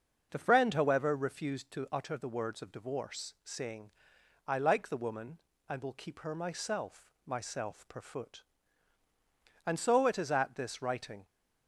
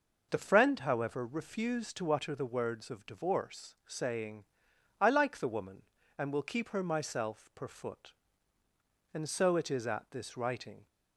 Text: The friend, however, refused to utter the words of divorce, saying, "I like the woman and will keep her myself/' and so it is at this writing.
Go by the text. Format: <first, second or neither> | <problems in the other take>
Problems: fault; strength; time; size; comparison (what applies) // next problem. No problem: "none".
second | starts louder than the rest; noticeable; until 1.3 s; 6 dB // says "myself" twice; at 7.2 s